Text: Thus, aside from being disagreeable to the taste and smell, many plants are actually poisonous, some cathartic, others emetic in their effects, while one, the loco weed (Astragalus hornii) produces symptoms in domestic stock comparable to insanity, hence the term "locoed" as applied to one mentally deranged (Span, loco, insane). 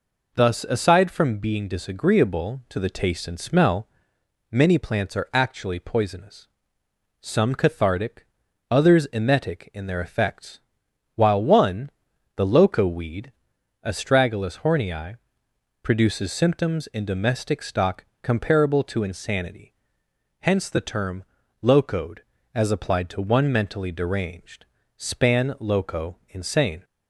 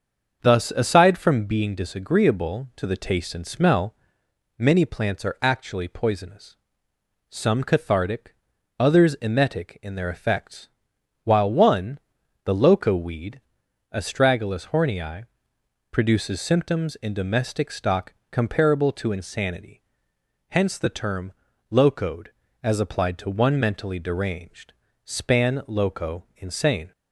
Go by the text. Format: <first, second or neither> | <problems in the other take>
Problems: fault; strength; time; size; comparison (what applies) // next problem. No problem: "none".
first | starts louder than the rest; until 1.8 s; 6.5 dB // pauses between "stock" and "comparable"; slight; at 18.1 s; 0.16 s long; slight in the first // pauses between "term" and "locoed"; at 21.3 s; 0.40 s long; also in the first